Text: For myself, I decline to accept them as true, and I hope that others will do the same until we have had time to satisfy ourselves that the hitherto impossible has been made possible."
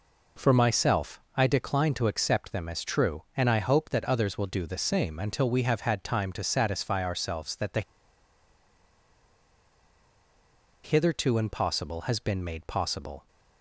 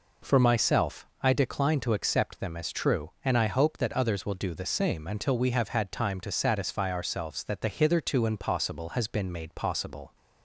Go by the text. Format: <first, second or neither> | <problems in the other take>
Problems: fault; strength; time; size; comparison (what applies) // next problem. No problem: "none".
second | pauses between "the" and "hitherto"; strong; at 7.8 s; 3.0 s long